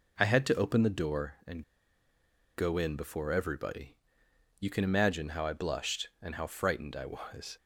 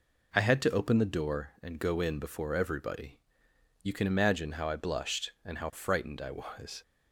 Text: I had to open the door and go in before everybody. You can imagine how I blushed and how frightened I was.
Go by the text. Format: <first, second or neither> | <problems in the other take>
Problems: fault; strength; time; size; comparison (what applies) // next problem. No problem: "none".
second | pauses between "and" and "go"; noticeable; at 1.6 s; 0.95 s long